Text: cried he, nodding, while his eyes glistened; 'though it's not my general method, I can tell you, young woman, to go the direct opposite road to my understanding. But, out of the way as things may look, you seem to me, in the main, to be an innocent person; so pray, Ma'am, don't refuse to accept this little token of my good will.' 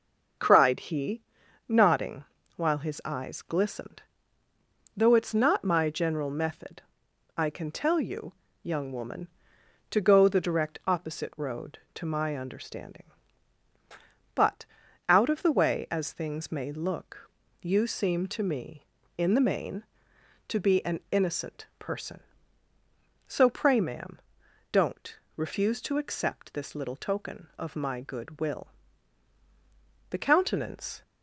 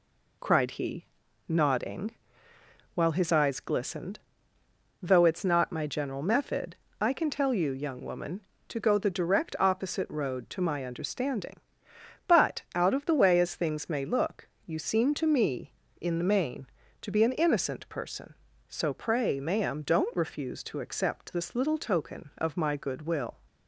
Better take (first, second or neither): second